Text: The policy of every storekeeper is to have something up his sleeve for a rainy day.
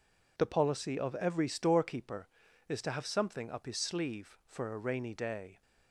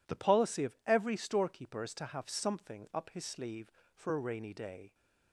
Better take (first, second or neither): neither